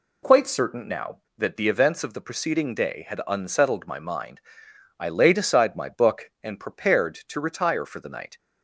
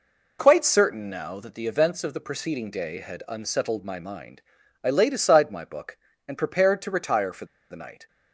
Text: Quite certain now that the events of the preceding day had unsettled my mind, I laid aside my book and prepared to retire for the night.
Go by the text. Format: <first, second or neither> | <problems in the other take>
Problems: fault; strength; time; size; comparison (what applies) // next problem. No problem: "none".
first | pauses between "for" and "the"; slight; at 7.4 s; 0.26 s long